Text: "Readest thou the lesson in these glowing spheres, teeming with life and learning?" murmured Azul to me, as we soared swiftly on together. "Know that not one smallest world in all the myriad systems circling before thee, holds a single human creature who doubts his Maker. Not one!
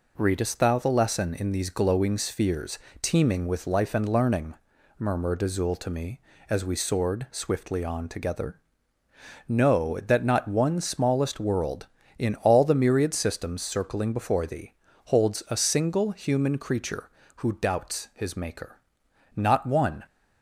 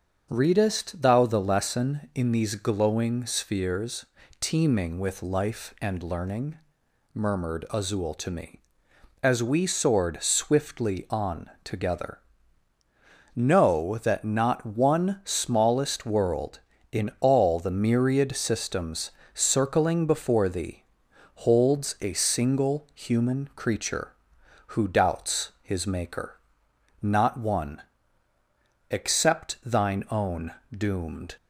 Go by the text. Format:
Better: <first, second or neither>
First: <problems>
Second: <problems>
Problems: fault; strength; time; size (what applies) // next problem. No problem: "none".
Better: first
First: none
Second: starts louder than the rest; until 1.3 s; 6.5 dB // pauses between "systems" and "circling"; slight; at 19.0 s; 0.24 s long // goes on to say "except thine own doomed"; strong; from 28.9 s on; 2.4 s long